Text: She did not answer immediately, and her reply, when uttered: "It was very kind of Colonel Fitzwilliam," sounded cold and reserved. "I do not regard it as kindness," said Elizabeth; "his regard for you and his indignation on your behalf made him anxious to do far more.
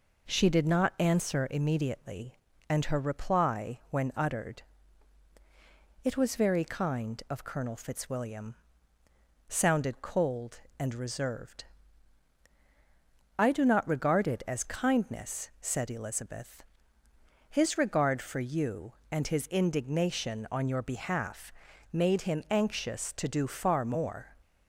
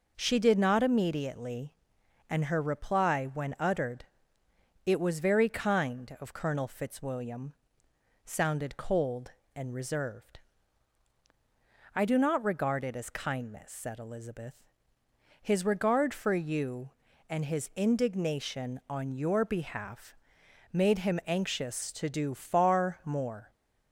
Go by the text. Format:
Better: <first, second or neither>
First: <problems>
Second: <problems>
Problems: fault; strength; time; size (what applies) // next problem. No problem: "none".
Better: first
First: pauses between "behalf" and "made"; at 21.5 s; 0.40 s long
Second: skips "answer"; at 0.8 s // pauses between "behalf" and "made"; noticeable; at 20.1 s; 0.56 s long